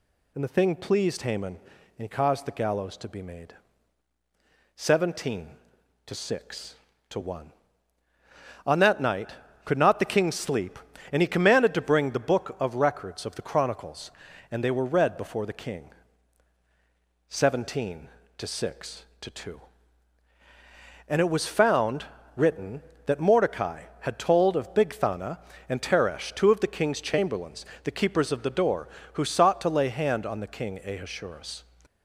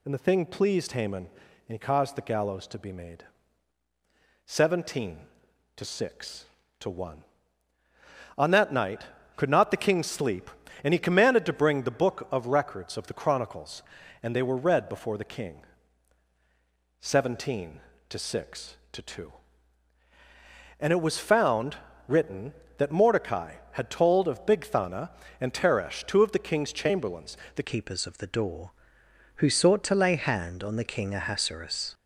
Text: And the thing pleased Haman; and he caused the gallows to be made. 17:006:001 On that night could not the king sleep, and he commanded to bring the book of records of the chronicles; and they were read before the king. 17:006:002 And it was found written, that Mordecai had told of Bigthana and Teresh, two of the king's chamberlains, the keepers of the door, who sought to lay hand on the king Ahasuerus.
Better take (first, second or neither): first